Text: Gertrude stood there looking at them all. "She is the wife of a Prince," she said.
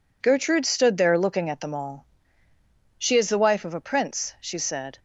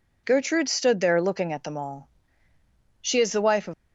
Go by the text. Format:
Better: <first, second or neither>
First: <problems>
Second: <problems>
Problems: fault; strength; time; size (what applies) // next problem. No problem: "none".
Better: first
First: none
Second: stops before "a Prince she said"; at 3.7 s